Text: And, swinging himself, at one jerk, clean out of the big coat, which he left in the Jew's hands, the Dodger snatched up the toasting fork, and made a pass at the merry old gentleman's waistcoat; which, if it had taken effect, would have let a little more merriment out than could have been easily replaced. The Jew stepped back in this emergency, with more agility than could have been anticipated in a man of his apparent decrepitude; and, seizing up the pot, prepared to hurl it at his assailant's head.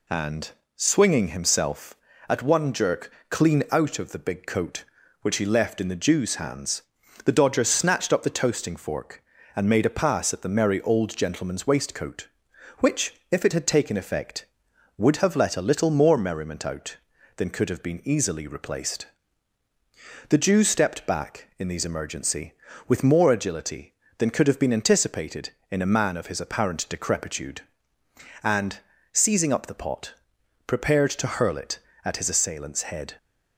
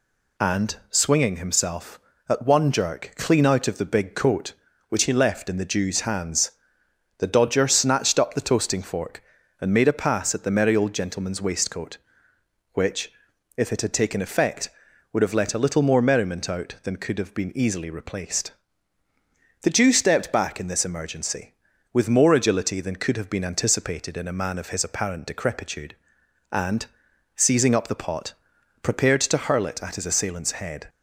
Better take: second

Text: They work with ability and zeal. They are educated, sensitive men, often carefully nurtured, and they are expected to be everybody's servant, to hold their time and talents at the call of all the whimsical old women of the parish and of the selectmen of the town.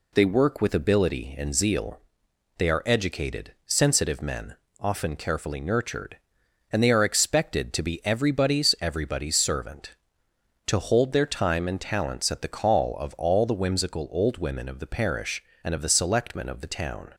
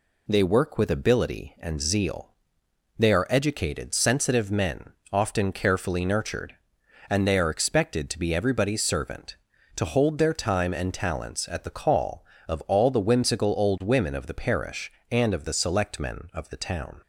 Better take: second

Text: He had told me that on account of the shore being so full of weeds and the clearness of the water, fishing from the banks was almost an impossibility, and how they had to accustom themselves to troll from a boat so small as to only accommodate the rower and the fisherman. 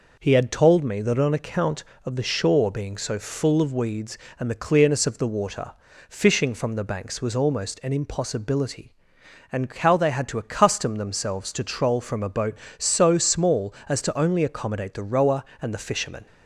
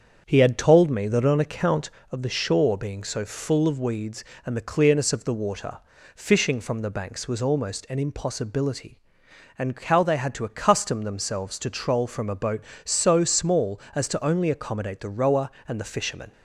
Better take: first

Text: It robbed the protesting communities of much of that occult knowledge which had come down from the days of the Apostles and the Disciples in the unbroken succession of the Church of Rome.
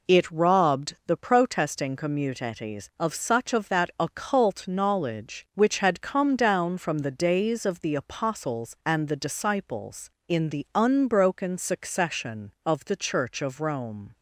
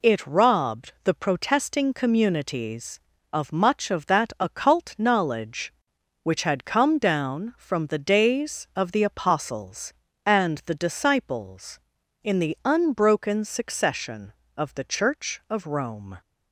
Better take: second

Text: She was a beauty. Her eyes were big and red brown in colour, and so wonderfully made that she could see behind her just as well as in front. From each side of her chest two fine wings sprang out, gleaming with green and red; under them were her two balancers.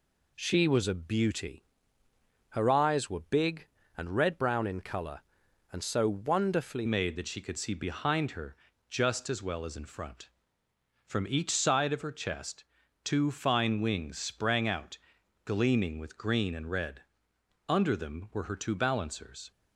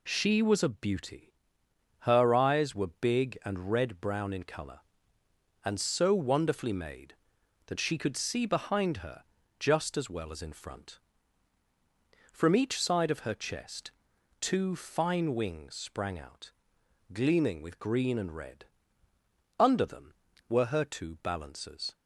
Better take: second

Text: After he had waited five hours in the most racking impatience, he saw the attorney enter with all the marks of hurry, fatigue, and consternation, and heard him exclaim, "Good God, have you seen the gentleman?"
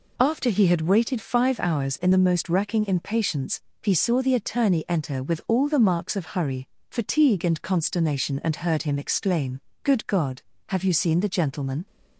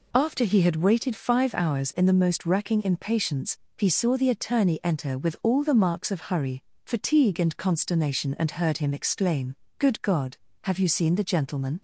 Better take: neither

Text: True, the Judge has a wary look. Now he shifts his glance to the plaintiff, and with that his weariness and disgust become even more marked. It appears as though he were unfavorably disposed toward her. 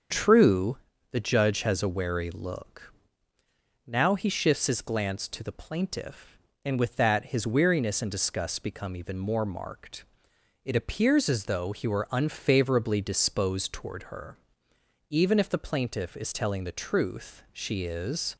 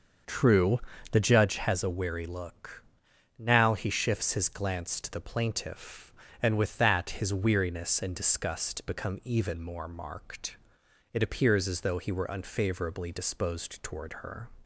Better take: second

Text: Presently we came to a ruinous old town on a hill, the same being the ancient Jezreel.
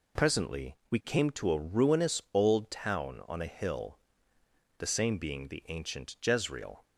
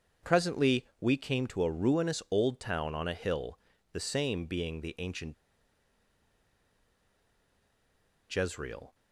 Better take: first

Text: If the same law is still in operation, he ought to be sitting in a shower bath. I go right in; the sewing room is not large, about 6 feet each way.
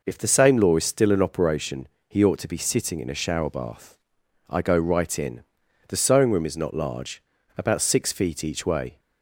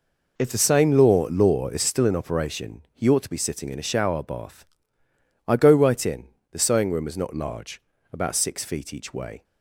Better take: first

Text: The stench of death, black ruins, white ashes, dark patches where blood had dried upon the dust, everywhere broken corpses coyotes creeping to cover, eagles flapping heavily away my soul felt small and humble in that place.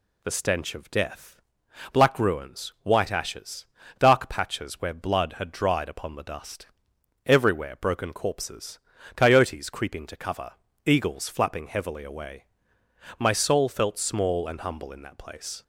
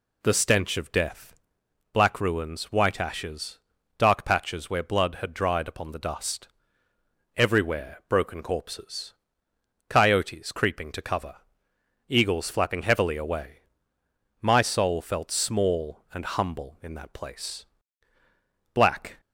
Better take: first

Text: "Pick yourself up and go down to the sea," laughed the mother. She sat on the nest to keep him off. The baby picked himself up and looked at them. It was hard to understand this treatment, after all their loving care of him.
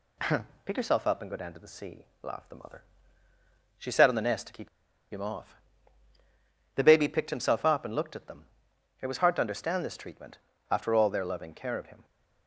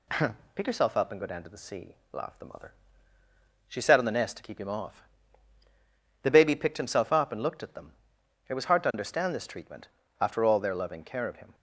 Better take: second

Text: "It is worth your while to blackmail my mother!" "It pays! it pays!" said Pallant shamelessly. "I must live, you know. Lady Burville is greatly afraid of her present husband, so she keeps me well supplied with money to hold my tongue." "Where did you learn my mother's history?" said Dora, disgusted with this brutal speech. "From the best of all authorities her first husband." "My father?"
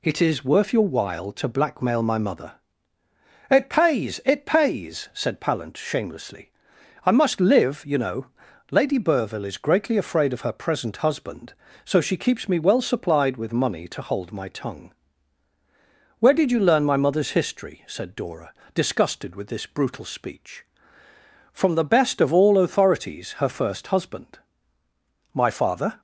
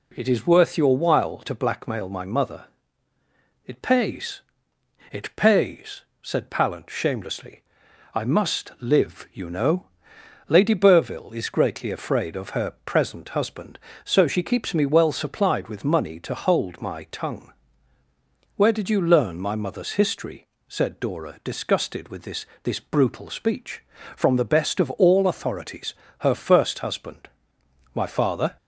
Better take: first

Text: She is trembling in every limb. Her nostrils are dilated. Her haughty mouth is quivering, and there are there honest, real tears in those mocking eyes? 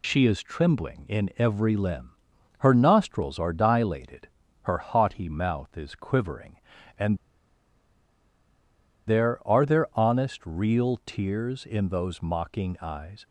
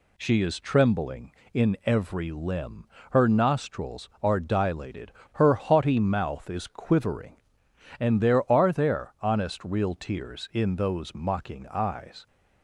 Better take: second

